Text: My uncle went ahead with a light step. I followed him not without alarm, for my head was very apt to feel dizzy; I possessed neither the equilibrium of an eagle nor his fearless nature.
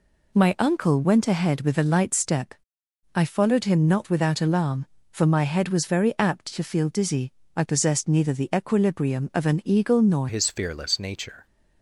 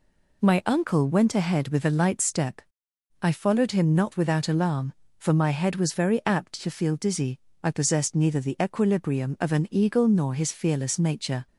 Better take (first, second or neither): second